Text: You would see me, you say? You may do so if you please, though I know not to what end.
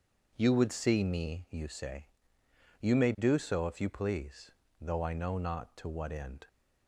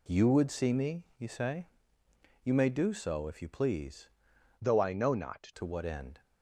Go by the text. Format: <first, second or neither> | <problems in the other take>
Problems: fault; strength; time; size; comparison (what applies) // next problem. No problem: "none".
first | changes voice from "though" to "not"; from 4.6 to 5.5 s; 0.9 s long